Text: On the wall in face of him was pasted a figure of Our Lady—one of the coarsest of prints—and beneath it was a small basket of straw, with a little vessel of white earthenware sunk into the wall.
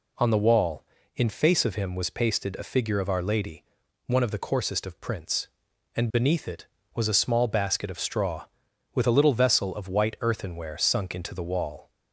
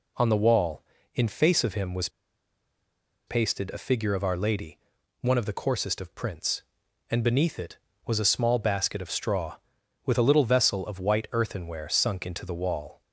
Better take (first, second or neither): first